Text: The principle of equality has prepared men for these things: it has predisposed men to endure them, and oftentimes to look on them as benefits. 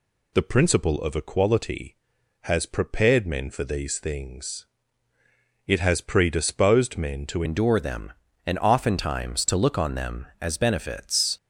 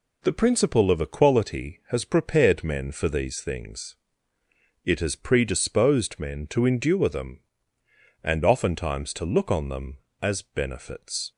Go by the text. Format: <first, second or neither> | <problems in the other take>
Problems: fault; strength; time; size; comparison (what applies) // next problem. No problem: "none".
second | changes voice at "endure"; from 7.4 s on; 3.9 s long